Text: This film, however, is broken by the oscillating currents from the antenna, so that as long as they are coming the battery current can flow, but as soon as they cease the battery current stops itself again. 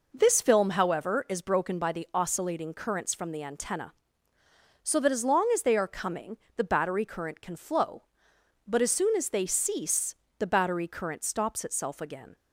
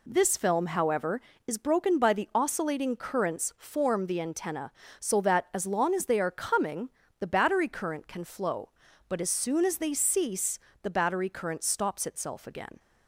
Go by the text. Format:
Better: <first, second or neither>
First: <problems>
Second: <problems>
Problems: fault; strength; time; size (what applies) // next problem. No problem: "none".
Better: first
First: pauses between "coming" and "the"; slight; at 6.3 s; 0.18 s long // pauses between "cease" and "the"; slight; at 10.1 s; 0.22 s long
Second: says "form" for "from"; at 3.5 s // pauses between "coming" and "the"; slight; at 6.8 s; 0.30 s long // pauses between "cease" and "the"; slight; at 10.5 s; 0.24 s long